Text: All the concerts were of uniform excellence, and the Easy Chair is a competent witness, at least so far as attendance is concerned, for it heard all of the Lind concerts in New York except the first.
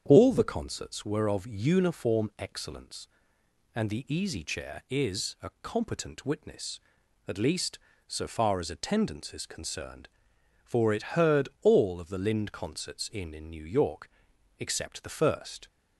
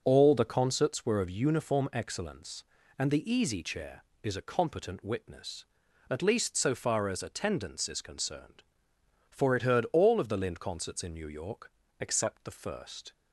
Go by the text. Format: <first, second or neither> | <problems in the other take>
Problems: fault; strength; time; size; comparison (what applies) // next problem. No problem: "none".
second | starts louder than the rest; strong; until 1.0 s; 8 dB; noticeable in the second // says "in" twice; at 13.3 s // pauses between "York" and "except"; noticeable; at 14.0 s; 0.50 s long; slight in the second